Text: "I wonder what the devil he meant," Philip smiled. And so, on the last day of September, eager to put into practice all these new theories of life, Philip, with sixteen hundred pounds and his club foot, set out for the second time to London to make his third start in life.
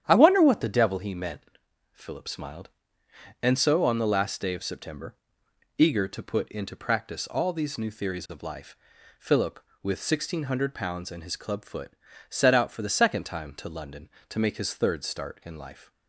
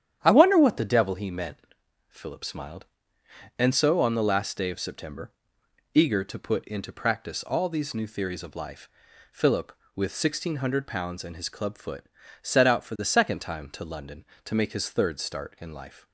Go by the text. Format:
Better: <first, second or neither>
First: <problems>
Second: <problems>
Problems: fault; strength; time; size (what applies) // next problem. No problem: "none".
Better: neither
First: starts louder than the rest; strong; until 1.0 s; 10 dB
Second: starts louder than the rest; strong; until 1.2 s; 10 dB